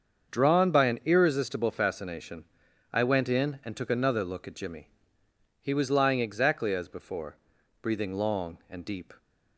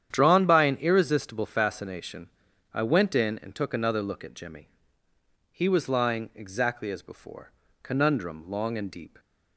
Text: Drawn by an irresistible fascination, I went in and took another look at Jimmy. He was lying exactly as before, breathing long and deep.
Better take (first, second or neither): first